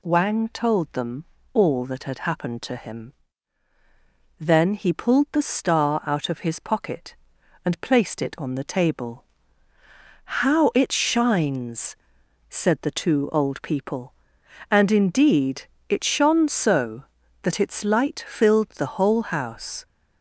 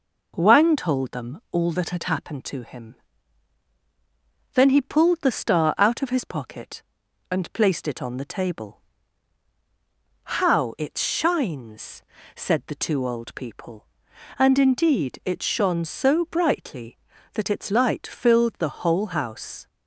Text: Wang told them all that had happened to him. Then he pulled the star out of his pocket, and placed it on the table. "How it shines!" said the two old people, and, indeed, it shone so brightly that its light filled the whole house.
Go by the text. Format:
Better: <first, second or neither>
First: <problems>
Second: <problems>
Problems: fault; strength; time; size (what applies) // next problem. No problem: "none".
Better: second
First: pauses between "them" and "all"; slight; at 1.2 s; 0.28 s long // skips "brightly"; at 17.2 s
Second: none